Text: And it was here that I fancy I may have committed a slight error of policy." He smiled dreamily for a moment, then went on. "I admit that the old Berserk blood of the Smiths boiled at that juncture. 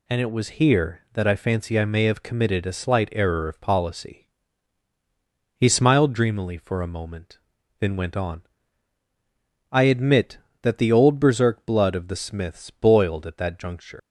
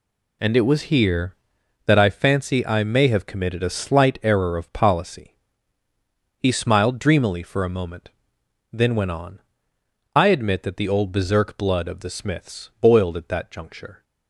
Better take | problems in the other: second | leaves "juncture" unfinished; at 13.9 s; 125 ms

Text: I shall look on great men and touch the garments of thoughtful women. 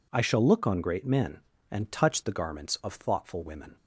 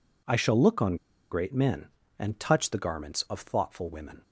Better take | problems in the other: first | pauses between "on" and "great"; at 0.9 s; 0.36 s long

